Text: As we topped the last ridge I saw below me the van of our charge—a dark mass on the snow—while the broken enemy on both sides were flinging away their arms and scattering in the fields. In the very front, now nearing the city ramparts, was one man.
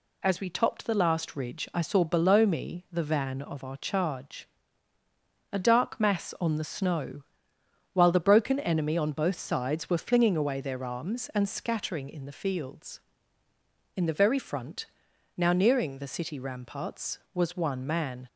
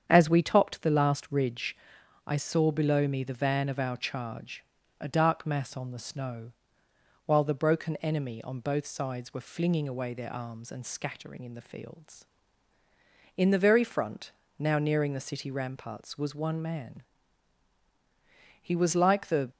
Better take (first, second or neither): first